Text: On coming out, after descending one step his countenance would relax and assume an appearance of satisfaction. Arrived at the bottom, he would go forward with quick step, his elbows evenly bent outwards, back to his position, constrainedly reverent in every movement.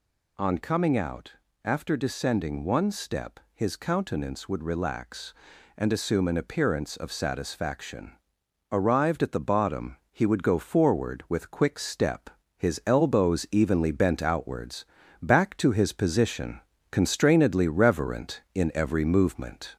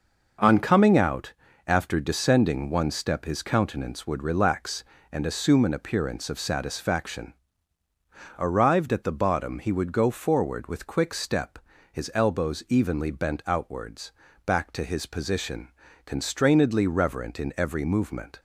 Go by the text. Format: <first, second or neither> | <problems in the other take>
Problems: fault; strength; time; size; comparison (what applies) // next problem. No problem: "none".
second | gets louder; slight; throughout; 2.5 dB // pauses between "step" and "his"; slight; at 3.3 s; 0.16 s long